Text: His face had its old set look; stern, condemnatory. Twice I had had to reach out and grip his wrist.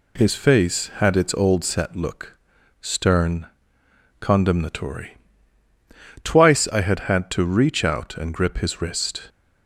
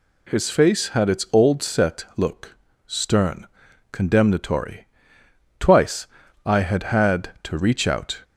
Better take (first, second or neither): first